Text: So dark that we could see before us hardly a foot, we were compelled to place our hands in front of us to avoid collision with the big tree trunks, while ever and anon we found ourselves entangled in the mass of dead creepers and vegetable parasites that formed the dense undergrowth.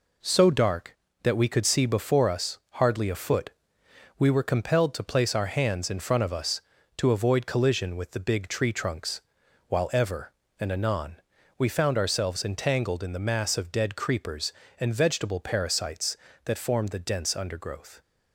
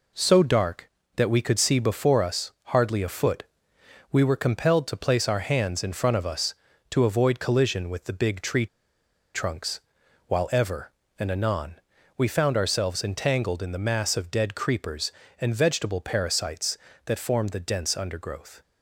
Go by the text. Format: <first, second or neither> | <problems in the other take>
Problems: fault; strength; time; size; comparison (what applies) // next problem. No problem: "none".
first | pauses between "tree" and "trunks"; noticeable; at 8.6 s; 0.67 s long // pauses between "anon" and "we"; at 11.7 s; 0.42 s long; also in the first